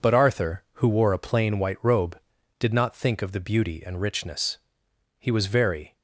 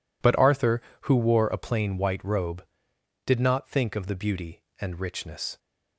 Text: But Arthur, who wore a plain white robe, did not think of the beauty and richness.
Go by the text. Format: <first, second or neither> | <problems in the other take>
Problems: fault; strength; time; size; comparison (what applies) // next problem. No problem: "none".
second | goes on to say "He was very"; noticeable; from 5.1 s on; 0.76 s long